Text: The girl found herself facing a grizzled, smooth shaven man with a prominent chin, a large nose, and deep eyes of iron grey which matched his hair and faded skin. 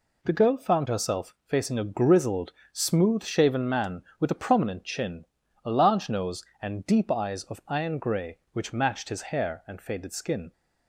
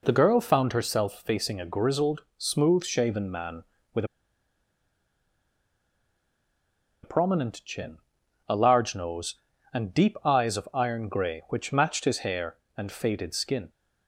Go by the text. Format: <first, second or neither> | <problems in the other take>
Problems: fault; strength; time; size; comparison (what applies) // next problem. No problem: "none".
first | pauses between "with" and "a"; strong; at 4.0 s; 2.9 s long